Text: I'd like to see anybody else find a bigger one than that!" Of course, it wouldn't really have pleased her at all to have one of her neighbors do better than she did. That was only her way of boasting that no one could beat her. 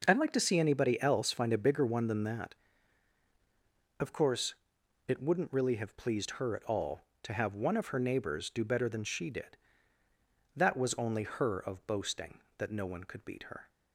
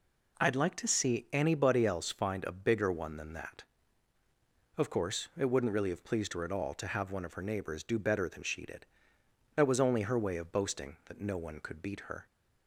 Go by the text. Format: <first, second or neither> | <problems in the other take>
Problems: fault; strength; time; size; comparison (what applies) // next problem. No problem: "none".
second | skips "way"; at 11.5 s